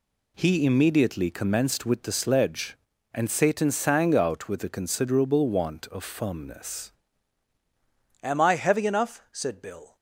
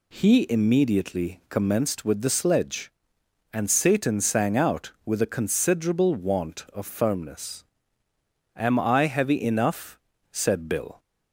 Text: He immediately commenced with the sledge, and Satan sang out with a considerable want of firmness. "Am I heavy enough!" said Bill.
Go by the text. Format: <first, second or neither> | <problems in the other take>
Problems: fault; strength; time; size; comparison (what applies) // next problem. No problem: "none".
second | changes voice at "Am"; from 8.2 s on; 1.7 s long